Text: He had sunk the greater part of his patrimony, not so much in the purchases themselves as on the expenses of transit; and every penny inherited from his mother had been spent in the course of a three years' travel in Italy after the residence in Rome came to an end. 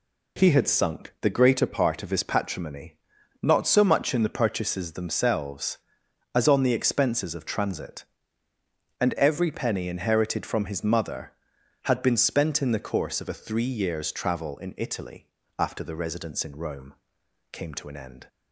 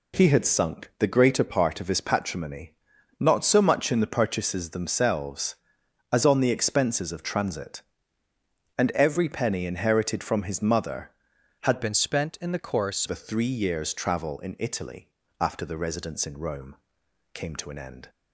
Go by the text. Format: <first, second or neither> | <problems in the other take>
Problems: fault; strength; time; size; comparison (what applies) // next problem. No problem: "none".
first | changes voice from "been" to "course"; from 11.8 to 13.0 s; 1.2 s long // pauses between "Italy" and "after"; slight; at 15.0 s; 0.32 s long; slight in the first // pauses between "Rome" and "came"; noticeable; at 16.7 s; 0.60 s long; noticeable in the first